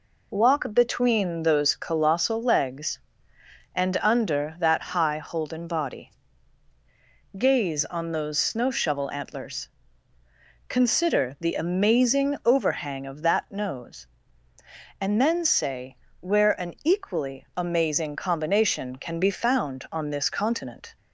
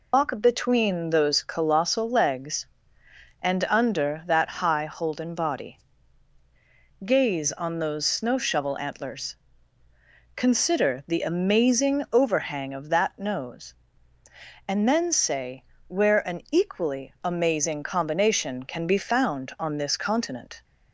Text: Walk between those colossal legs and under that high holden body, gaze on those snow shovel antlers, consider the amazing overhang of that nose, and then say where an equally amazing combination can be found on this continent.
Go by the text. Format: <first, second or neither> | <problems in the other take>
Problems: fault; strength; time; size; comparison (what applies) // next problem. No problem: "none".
first | loses the start of "Walk"; at 0.1 s; 140 ms // pauses between "say" and "where"; slight; at 15.6 s; 0.22 s long; slight in the first